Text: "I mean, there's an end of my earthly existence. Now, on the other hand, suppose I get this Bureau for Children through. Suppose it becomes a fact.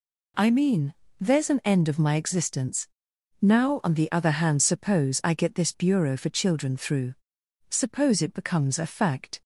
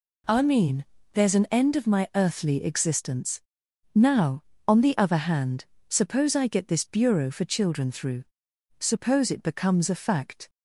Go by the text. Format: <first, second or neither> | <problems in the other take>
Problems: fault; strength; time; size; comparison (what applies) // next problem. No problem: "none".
second | skips "earthly"; at 2.1 s